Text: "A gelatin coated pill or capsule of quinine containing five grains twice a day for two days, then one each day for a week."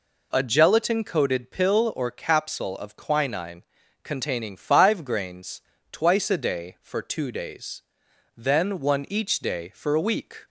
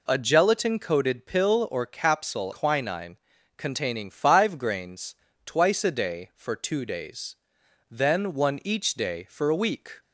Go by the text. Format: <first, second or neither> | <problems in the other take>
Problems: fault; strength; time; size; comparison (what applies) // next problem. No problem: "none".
first | skips "of"; at 2.5 s // pauses between "quinine" and "containing"; at 3.1 s; 0.40 s long; also in the first // pauses between "grains" and "twice"; slight; at 5.1 s; 0.30 s long; slight in the first